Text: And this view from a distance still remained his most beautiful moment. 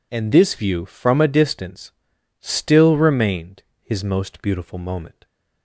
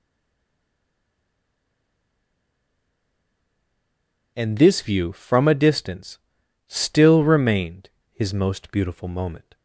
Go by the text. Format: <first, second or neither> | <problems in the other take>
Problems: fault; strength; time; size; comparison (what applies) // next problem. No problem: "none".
first | stays silent before the first word; strong; until 4.3 s; 4.3 s long // pauses between "distance" and "still"; noticeable; at 6.1 s; 0.48 s long; noticeable in the first // pauses between "remained" and "his"; slight; at 7.8 s; 0.22 s long; slight in the first